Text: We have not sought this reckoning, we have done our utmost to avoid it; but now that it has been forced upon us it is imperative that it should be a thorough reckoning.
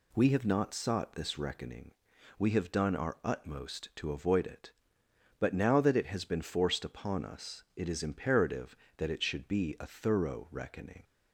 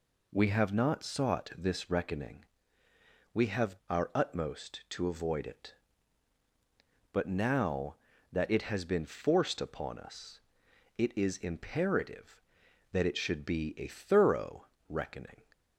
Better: first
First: none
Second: skips "done"; at 3.8 s // pauses between "us" and "it"; noticeable; at 10.4 s; 0.56 s long // pauses between "thorough" and "reckoning"; slight; at 14.6 s; 0.24 s long

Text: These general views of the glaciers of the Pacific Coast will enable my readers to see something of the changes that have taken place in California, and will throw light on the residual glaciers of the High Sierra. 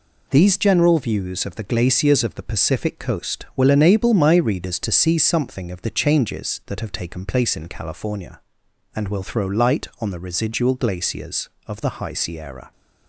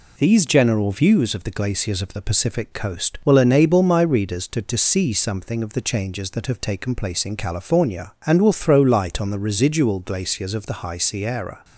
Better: first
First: none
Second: says "to" twice; at 4.6 s

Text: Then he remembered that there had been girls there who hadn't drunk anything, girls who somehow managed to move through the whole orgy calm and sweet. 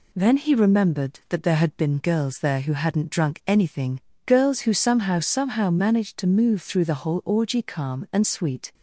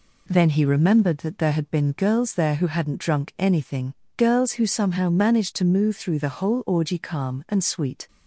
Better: second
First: says "somehow" twice; at 5.2 s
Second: none

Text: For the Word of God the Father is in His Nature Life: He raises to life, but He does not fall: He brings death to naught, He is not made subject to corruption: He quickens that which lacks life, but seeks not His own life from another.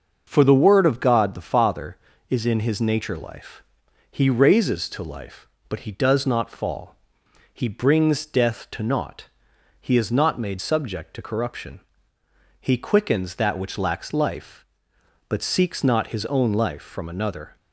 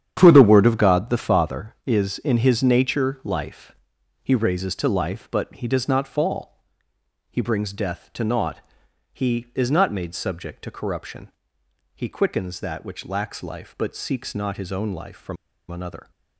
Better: first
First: starts louder than the rest; until 1.2 s; 6 dB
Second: starts louder than the rest; strong; until 1.1 s; 9 dB // pauses between "from" and "another"; slight; at 15.3 s; 0.34 s long

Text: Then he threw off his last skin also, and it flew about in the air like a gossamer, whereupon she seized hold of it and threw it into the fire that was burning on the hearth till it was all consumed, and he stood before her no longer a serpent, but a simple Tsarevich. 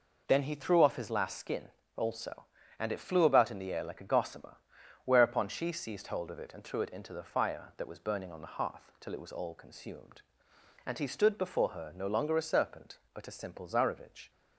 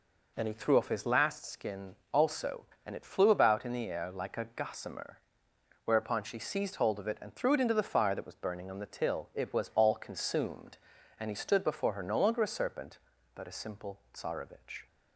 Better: first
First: pauses between "skin" and "also"; slight; at 1.6 s; 0.26 s long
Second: pauses between "skin" and "also"; slight; at 1.9 s; 0.16 s long // skips "hearth"; at 8.8 s

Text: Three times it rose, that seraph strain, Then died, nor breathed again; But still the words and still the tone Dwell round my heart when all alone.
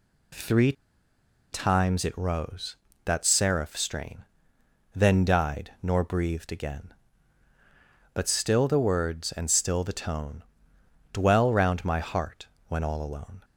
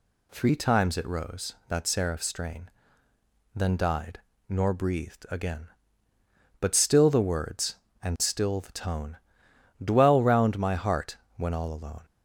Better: second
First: pauses between "Three" and "times"; noticeable; at 0.7 s; 0.78 s long // pauses between "tone" and "Dwell"; noticeable; at 10.4 s; 0.68 s long // pauses between "heart" and "when"; slight; at 12.4 s; 0.22 s long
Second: pauses between "tone" and "Dwell"; noticeable; at 9.1 s; 0.64 s long // pauses between "heart" and "when"; slight; at 11.1 s; 0.20 s long

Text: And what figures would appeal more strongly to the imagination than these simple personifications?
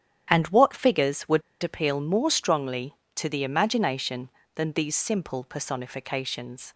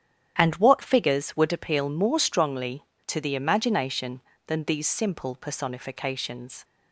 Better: second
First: starts louder than the rest; strong; until 1.3 s; 9.5 dB // pauses between "would" and "appeal"; slight; at 1.4 s; 0.20 s long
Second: starts louder than the rest; strong; until 1.4 s; 9.5 dB

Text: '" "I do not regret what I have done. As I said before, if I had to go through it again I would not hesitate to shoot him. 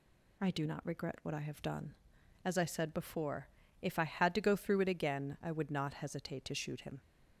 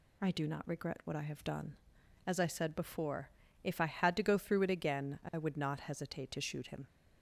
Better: neither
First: none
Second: none

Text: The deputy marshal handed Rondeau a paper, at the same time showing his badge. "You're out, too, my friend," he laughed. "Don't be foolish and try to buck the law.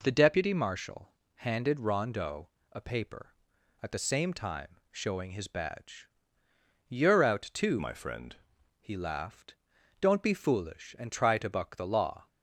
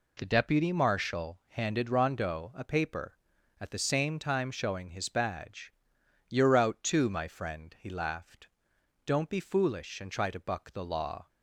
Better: second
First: pauses between "marshal" and "handed"; slight; at 1.1 s; 0.24 s long // pauses between "Rondeau" and "a"; slight; at 2.4 s; 0.24 s long // changes voice from "my" to "friend"; from 7.7 to 8.3 s; 0.6 s long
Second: none

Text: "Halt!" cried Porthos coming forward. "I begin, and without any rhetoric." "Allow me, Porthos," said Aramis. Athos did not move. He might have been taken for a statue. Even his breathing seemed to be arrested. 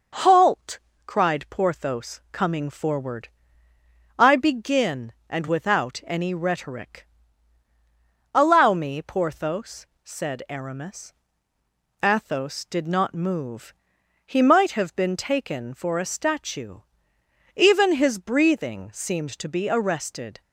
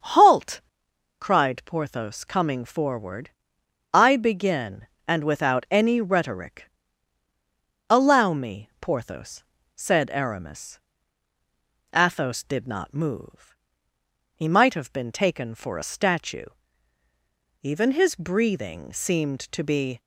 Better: first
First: none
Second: starts louder than the rest; until 1.6 s; 6.5 dB // stops before "arrested"; at 19.9 s

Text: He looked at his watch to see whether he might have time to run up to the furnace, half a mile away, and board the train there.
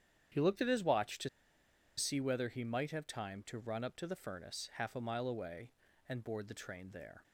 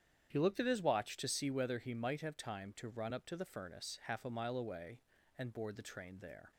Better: second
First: starts louder than the rest; strong; until 2.0 s; 9 dB // pauses between "to" and "see"; noticeable; at 1.2 s; 0.68 s long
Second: starts louder than the rest; strong; until 1.3 s; 9 dB

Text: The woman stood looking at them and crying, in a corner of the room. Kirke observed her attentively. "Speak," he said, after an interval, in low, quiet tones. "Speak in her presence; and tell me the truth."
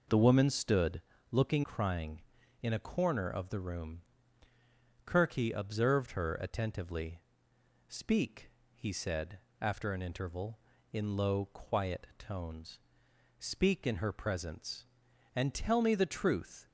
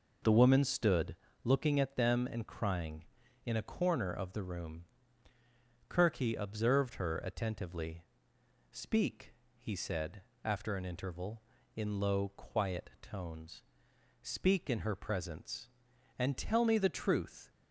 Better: second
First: pauses between "stood" and "looking"; slight; at 1.0 s; 0.30 s long // skips "at them and"; at 1.6 s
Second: pauses between "stood" and "looking"; slight; at 1.1 s; 0.28 s long

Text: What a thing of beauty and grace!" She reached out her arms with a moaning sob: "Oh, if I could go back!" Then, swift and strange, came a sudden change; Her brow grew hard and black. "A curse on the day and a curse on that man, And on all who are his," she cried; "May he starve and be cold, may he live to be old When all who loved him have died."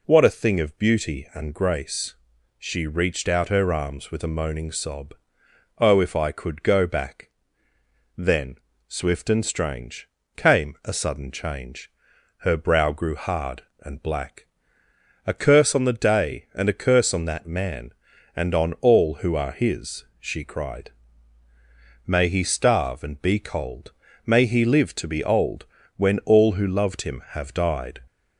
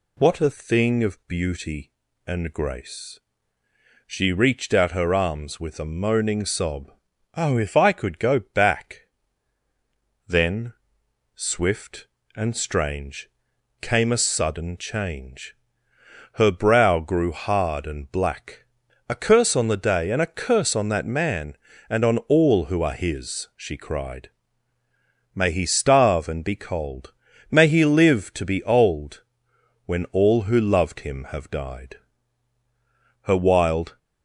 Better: first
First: pauses between "old" and "When"; slight; at 25.6 s; 0.32 s long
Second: pauses between "old" and "When"; noticeable; at 29.2 s; 0.64 s long // goes on to say "Her wild"; noticeable; from 33.2 s on; 0.76 s long

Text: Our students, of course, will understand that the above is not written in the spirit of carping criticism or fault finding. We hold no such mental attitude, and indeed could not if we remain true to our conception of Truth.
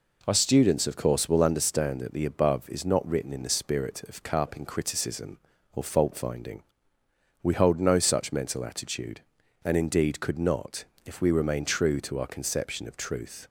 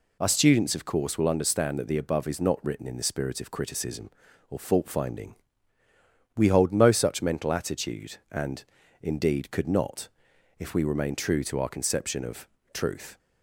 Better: first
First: pauses between "not" and "if"; slight; at 10.8 s; 0.20 s long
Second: skips "carping"; at 3.4 s // pauses between "and" and "indeed"; at 8.6 s; 0.38 s long // pauses between "not" and "if"; noticeable; at 10.0 s; 0.50 s long // pauses between "of" and "Truth"; slight; at 12.4 s; 0.24 s long

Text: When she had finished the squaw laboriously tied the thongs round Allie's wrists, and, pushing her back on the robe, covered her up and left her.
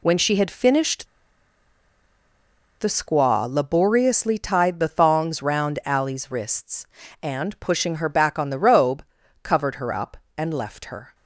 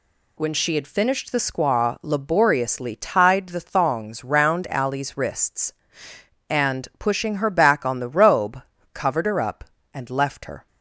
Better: second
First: pauses between "finished" and "the"; strong; at 1.0 s; 1.7 s long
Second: none

